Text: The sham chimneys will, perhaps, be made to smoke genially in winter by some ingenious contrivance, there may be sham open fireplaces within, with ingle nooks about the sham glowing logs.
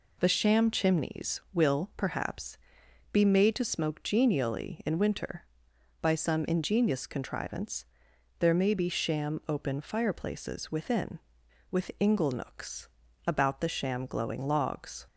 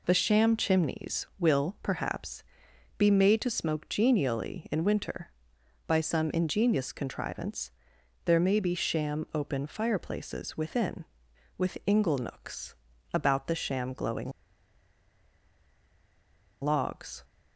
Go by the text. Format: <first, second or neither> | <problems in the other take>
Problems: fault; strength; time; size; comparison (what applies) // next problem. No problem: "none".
first | pauses between "nooks" and "about"; at 12.7 s; 0.40 s long; also in the first // pauses between "glowing" and "logs"; strong; at 14.3 s; 2.3 s long